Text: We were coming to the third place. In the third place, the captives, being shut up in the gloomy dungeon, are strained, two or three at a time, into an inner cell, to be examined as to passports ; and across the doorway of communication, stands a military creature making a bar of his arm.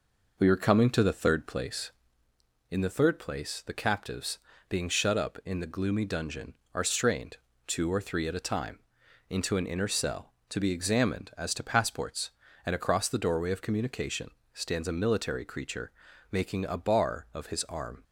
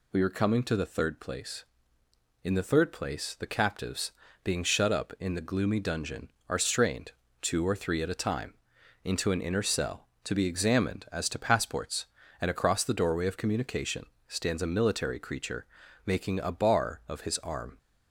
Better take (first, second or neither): second